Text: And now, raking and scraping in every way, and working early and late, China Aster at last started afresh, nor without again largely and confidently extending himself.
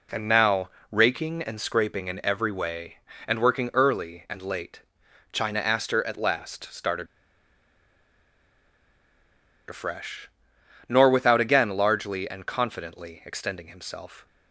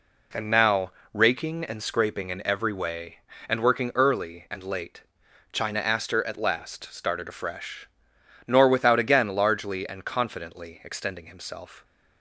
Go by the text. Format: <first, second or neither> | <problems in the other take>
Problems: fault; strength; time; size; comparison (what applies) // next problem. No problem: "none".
second | pauses between "started" and "afresh"; strong; at 7.0 s; 2.6 s long